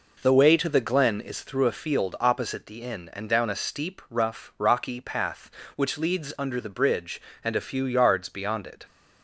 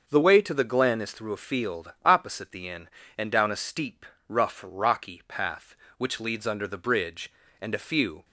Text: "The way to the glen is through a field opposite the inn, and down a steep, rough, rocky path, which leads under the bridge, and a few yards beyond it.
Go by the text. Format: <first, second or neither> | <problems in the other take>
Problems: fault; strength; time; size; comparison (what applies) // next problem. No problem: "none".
first | starts louder than the rest; until 1.0 s; 6 dB // stops before "yards beyond it"; at 8.2 s